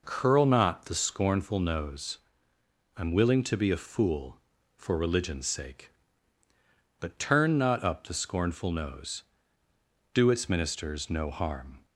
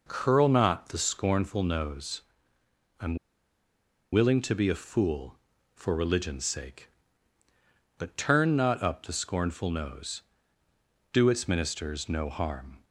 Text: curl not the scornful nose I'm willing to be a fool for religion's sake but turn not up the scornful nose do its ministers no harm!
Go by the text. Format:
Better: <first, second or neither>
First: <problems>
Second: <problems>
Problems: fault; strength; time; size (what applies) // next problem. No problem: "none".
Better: first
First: pauses between "nose" and "I'm"; noticeable; at 2.1 s; 0.78 s long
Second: pauses between "nose" and "I'm"; noticeable; at 2.2 s; 0.78 s long // pauses between "I'm" and "willing"; noticeable; at 3.1 s; 0.97 s long